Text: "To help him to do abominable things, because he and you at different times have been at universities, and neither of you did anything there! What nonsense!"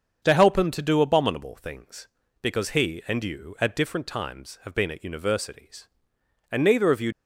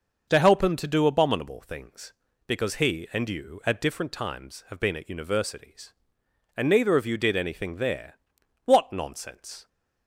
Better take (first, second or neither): second